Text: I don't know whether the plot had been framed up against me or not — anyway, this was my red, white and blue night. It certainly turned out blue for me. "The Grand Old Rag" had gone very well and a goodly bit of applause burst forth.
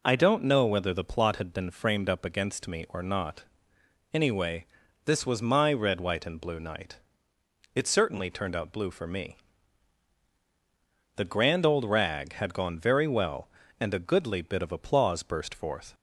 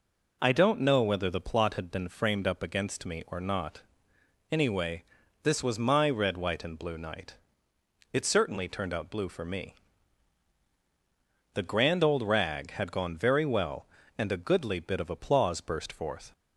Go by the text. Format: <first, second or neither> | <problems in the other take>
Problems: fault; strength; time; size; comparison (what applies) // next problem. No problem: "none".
neither | none